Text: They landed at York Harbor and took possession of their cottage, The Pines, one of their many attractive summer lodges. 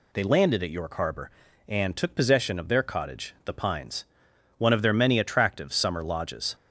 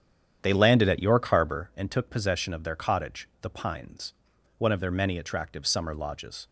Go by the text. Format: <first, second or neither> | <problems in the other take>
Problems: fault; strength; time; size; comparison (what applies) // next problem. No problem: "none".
first | starts louder than the rest; strong; until 1.7 s; 9 dB